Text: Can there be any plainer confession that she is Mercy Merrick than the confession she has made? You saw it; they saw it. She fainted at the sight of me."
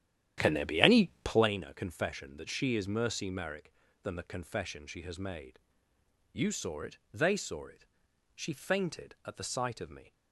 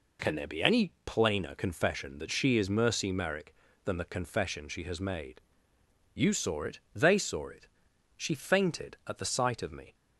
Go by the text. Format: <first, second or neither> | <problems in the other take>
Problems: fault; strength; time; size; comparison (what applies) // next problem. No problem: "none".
second | starts louder than the rest; strong; until 1.5 s; 11 dB // pauses between "any" and "plainer"; slight; at 1.0 s; 0.16 s long; slight in the second